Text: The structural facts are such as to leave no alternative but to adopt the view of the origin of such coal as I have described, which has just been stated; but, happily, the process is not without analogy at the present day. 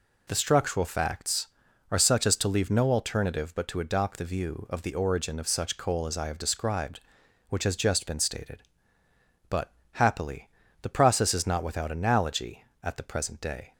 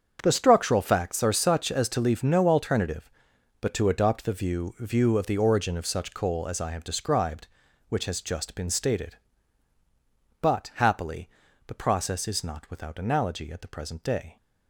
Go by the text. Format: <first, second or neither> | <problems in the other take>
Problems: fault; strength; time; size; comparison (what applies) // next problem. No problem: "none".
first | starts louder than the rest; until 1.2 s; 7 dB // says "view" twice; at 4.7 s